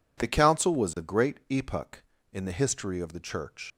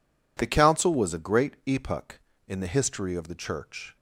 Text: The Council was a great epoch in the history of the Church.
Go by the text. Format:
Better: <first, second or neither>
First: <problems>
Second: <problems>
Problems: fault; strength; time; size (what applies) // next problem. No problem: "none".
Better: second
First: leaves "Church" unfinished; at 3.7 s; 110 ms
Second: none